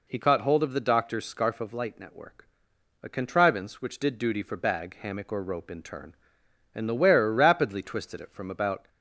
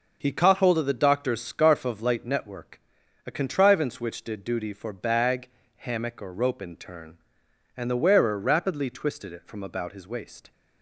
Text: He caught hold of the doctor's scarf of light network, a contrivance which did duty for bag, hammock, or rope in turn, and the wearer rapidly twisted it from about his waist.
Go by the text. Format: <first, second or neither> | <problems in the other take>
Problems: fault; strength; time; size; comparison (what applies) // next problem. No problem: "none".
second | stops before "his waist"; at 8.8 s